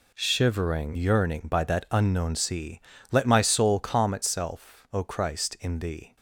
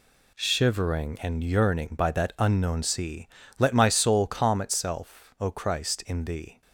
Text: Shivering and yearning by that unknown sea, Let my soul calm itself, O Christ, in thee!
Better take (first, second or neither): second